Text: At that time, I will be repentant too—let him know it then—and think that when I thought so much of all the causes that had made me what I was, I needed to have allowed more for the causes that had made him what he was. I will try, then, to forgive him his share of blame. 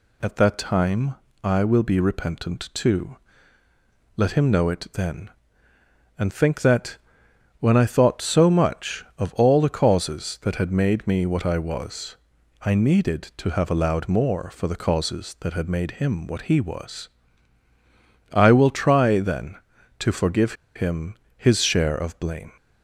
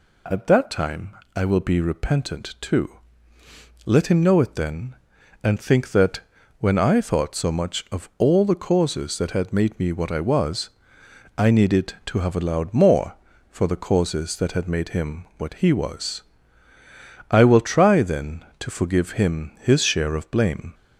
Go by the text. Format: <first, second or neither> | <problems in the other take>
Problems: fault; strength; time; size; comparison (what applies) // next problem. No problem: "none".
second | pauses between "that" and "when"; noticeable; at 6.9 s; 0.62 s long; also in the second // pauses between "forgive" and "him"; slight; at 20.5 s; 0.22 s long // pauses between "him" and "his"; slight; at 21.1 s; 0.20 s long